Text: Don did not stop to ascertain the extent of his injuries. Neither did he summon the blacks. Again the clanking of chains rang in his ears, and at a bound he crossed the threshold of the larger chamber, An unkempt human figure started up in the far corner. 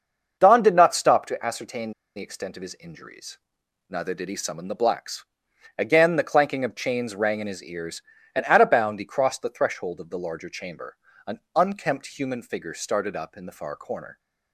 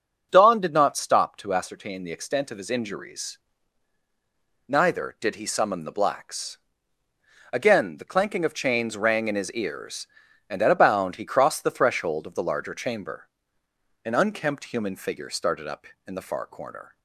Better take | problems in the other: second | starts louder than the rest; until 1.4 s; 6.5 dB; also in the second // pauses between "ascertain" and "the"; slight; at 1.9 s; 0.24 s long // pauses between "An" and "unkempt"; slight; at 11.3 s; 0.16 s long

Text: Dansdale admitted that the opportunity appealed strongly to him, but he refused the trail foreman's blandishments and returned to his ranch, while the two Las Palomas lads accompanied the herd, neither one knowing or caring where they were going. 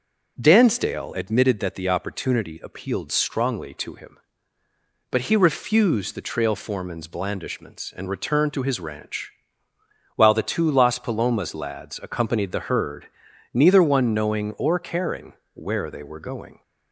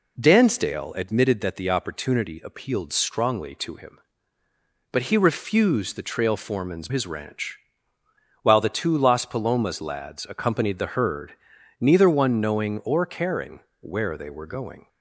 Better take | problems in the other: first | skips "blandishments and returned to"; at 6.8 s // pauses between "caring" and "where"; slight; at 13.6 s; 0.20 s long; slight in the first

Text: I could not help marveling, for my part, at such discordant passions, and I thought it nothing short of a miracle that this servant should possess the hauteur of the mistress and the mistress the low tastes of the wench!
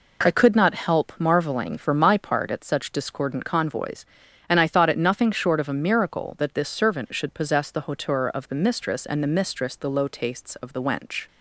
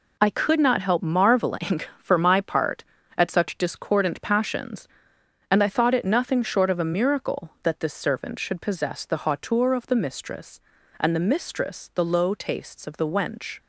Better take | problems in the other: second | says "convoys" for "passions"; at 3.4 s

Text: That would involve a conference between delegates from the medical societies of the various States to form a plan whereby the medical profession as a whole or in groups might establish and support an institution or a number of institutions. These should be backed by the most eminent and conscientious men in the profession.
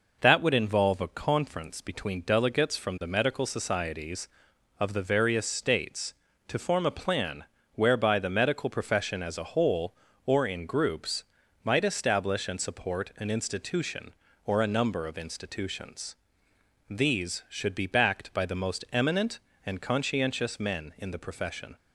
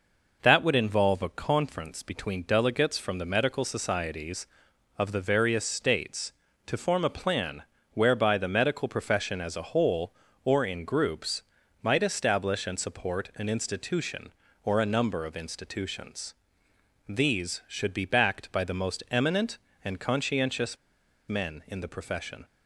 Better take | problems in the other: first | pauses between "plan" and "whereby"; slight; at 7.6 s; 0.28 s long; slight in the first // pauses between "groups" and "might"; at 11.4 s; 0.40 s long; also in the first // pauses between "conscientious" and "men"; noticeable; at 20.7 s; 0.51 s long

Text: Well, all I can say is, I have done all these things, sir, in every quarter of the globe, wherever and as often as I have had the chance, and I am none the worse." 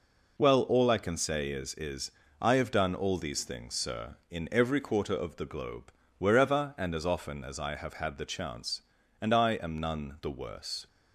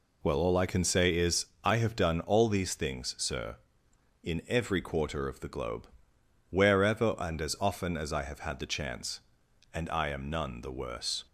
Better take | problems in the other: second | says "is" twice; at 1.7 s

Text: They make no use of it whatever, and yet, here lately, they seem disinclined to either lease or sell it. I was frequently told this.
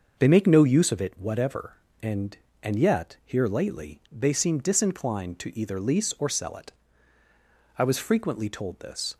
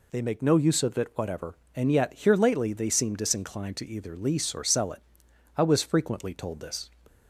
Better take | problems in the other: second | starts louder than the rest; until 1.2 s; 6.5 dB // says "and" twice; at 2.6 s

